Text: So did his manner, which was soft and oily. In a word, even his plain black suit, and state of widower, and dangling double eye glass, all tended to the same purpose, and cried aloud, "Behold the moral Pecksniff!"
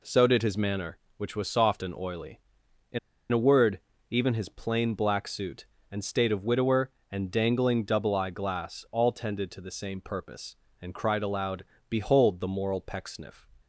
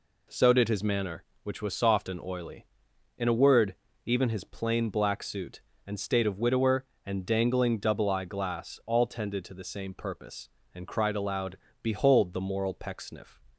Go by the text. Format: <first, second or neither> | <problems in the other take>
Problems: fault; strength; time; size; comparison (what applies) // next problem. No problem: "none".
second | pauses between "In" and "a"; slight; at 2.9 s; 0.32 s long